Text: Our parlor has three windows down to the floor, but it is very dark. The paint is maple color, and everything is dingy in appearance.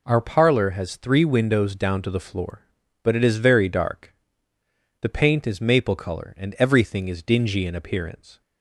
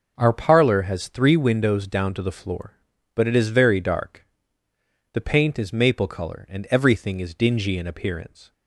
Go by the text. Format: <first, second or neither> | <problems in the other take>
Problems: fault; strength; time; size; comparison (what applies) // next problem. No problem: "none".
first | starts louder than the rest; noticeable; until 1.5 s; 5.5 dB